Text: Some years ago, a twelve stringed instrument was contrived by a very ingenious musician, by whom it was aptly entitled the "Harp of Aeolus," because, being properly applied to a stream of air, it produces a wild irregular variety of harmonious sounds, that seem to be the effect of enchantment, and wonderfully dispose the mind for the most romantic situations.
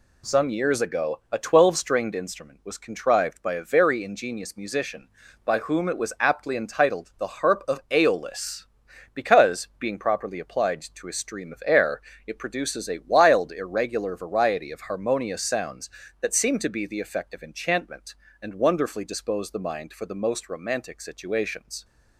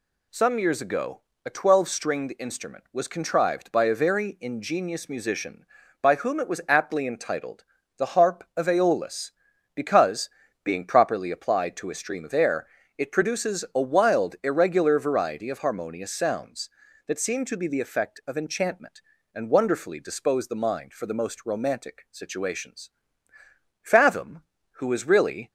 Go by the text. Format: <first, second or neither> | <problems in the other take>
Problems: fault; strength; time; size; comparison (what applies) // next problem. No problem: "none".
first | pauses between "entitled" and "the"; slight; at 7.6 s; 0.32 s long // goes on to say "Fathom who was really"; from 23.9 s on; 1.5 s long